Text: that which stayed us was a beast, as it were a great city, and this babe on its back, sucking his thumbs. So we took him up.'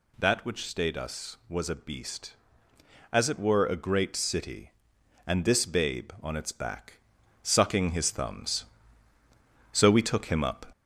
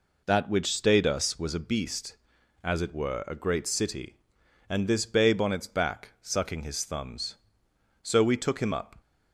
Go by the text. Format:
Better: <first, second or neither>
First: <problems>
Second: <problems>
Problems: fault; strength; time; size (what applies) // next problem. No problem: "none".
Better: second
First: gets louder; slight; throughout; 3 dB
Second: none